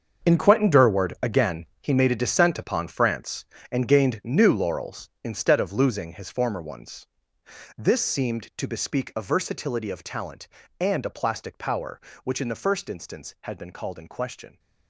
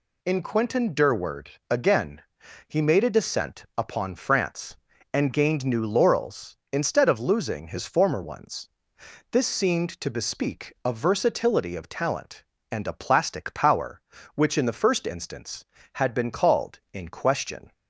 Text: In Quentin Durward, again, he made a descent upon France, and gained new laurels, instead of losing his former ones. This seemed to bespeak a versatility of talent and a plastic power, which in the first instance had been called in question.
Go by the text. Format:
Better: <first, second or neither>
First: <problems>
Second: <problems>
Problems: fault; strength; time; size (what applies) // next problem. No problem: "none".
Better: second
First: gets quieter; strong; throughout; 13 dB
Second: none